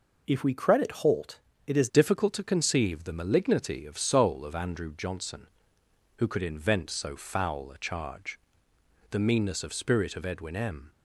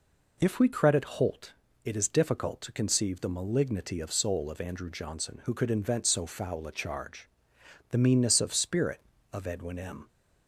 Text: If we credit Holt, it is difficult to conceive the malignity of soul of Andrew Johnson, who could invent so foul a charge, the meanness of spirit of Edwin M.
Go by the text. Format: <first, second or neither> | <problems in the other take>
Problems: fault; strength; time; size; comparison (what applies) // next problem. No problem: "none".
second | changes voice at "difficult"; from 1.8 s on; 9.1 s long